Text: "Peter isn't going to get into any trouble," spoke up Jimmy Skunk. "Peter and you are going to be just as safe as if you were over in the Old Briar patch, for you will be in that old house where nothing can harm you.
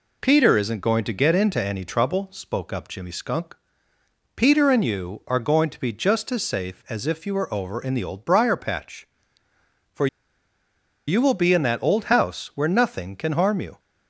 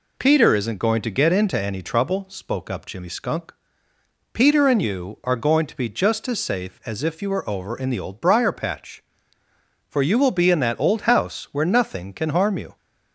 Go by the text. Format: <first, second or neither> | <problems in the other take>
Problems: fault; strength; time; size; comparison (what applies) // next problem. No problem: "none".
second | pauses between "for" and "you"; at 10.0 s; 1.0 s long